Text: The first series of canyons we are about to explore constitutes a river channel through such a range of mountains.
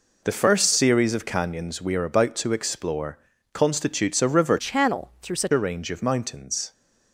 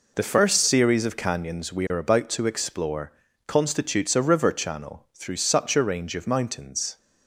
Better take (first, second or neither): second